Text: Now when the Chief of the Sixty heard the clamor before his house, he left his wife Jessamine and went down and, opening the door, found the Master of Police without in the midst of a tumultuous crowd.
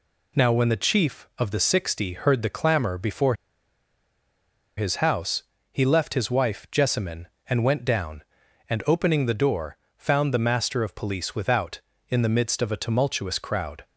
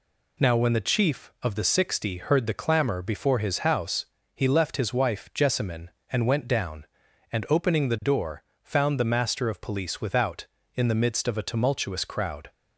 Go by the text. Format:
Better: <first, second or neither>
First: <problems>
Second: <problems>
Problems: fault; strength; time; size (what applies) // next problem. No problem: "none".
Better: second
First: pauses between "before" and "his"; strong; at 3.3 s; 1.4 s long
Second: none